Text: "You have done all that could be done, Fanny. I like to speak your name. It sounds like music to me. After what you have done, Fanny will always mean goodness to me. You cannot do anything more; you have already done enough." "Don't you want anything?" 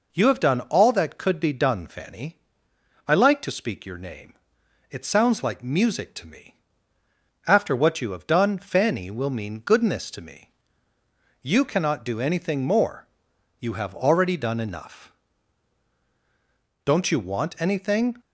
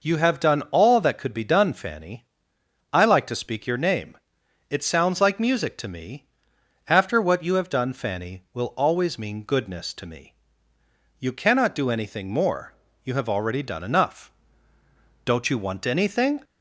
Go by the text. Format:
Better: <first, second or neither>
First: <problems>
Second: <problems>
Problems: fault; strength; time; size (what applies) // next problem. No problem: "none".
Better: second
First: skips "always"; at 9.3 s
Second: none